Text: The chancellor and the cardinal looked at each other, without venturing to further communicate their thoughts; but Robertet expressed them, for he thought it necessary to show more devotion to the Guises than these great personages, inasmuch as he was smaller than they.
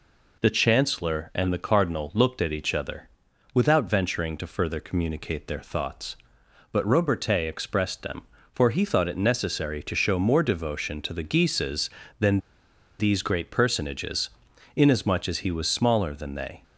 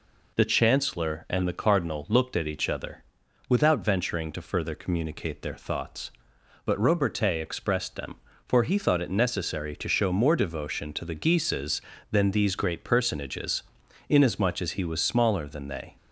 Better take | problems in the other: second | pauses between "than" and "these"; noticeable; at 12.3 s; 0.60 s long

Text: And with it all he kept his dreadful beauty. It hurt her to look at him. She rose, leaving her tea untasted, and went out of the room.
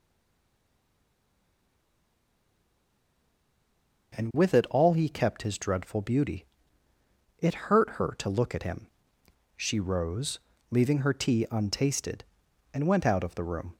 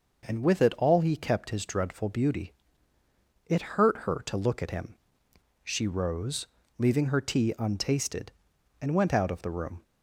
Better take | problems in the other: second | stays silent before the first word; strong; until 4.1 s; 4.1 s long

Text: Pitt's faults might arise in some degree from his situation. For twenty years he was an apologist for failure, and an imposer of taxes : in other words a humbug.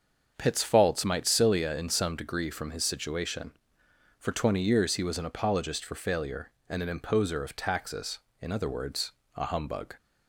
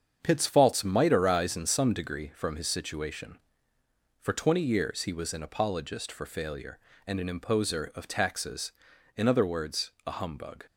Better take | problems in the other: second | starts louder than the rest; until 1.3 s; 7 dB; strong in the second // says "cilia" for "arise"; at 1.2 s // pauses between "words" and "a"; slight; at 9.1 s; 0.24 s long

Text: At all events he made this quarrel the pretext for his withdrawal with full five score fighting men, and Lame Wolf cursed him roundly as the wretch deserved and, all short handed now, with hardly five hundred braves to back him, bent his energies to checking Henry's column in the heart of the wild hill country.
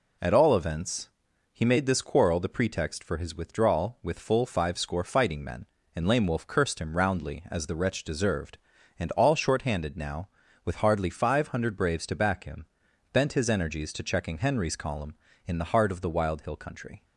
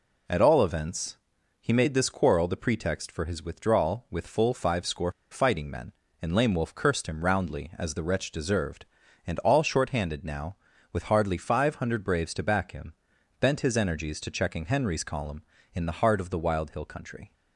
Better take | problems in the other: first | pauses between "events" and "he"; at 1.1 s; 0.42 s long; also in the first // pauses between "score" and "fighting"; slight; at 5.1 s; 0.18 s long

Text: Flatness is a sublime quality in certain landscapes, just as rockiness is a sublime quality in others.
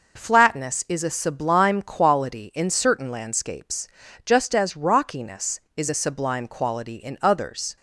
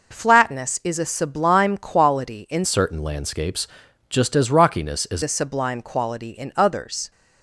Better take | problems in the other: first | changes voice from "certain" to "is"; from 2.6 to 5.2 s; 2.6 s long

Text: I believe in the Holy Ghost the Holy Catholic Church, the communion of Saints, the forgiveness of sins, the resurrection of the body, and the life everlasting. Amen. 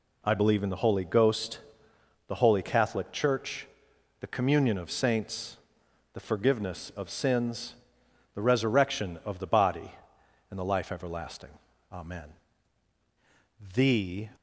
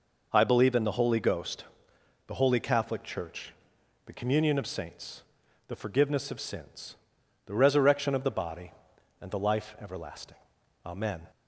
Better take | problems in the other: second | pauses between "Ghost" and "the"; noticeable; at 1.5 s; 0.68 s long; noticeable in the second // goes on to say "THE"; from 13.7 s on; 0.56 s long

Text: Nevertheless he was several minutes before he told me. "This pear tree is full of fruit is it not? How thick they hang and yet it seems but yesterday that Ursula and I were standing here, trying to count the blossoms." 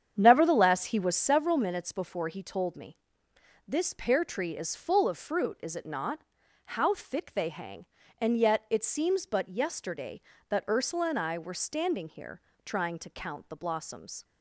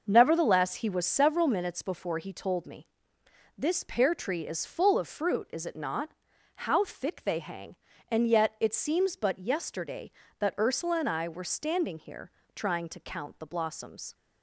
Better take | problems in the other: second | starts louder than the rest; strong; until 1.2 s; 8 dB

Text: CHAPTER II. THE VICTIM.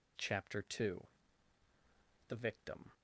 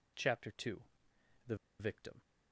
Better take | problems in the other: first | pauses between "THE" and "VICTIM"; slight; at 1.5 s; 0.23 s long

